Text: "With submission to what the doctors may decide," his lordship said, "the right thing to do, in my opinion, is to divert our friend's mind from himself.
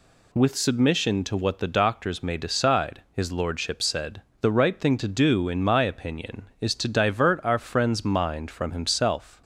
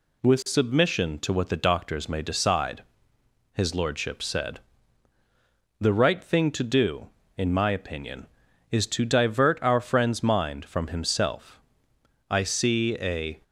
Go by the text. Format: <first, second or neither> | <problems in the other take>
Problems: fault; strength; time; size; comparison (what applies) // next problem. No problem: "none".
first | goes on to say "I see a"; noticeable; from 12.3 s on; 1.1 s long